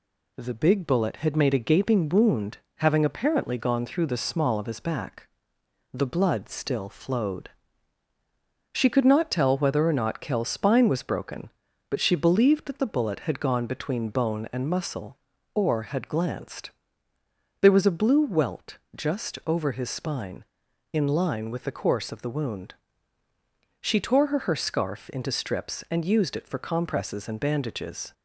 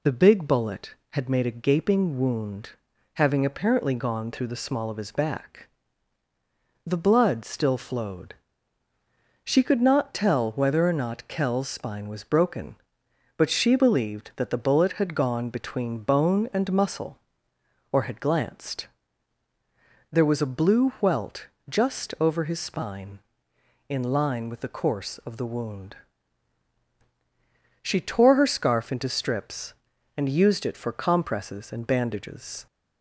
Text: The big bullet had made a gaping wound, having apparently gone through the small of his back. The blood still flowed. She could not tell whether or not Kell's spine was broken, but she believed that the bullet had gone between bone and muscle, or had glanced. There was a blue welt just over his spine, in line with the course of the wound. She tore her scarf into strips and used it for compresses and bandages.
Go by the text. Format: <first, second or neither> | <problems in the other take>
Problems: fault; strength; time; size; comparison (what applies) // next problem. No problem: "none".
second | pauses between "welt" and "just"; slight; at 18.7 s; 0.16 s long; slight in the second // says "her" twice; at 24.3 s